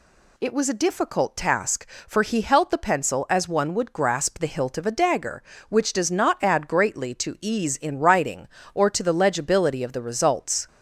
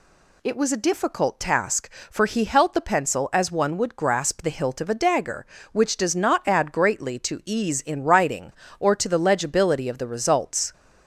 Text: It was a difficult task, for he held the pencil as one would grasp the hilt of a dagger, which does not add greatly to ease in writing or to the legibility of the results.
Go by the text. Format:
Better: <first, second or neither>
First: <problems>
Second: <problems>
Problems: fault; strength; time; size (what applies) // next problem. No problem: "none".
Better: neither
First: none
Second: none